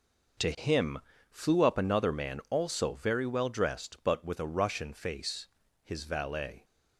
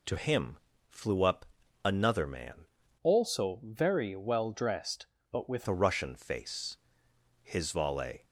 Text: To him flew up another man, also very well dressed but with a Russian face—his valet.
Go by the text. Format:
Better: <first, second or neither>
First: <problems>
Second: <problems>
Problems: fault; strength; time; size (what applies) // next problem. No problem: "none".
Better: first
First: pauses between "him" and "flew"; slight; at 1.0 s; 0.30 s long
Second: pauses between "him" and "flew"; slight; at 0.5 s; 0.32 s long // pauses between "up" and "another"; at 1.4 s; 0.40 s long // changes voice from "also" to "with"; from 3.0 to 5.6 s; 2.6 s long